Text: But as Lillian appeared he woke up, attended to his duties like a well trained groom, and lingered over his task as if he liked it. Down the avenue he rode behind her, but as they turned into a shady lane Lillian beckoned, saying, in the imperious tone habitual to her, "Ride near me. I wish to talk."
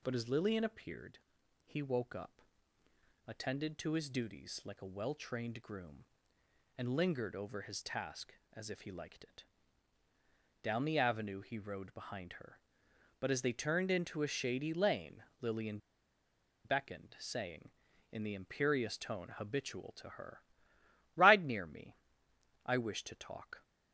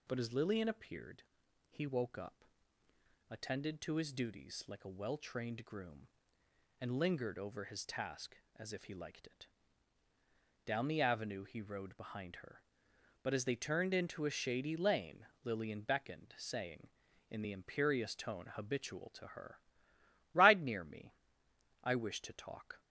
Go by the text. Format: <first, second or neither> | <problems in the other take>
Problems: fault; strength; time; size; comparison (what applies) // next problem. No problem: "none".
second | pauses between "appeared" and "he"; noticeable; at 1.1 s; 0.48 s long; noticeable in the second // pauses between "lane" and "Lillian"; slight; at 15.2 s; 0.16 s long; slight in the second // pauses between "Lillian" and "beckoned"; noticeable; at 15.7 s; 0.87 s long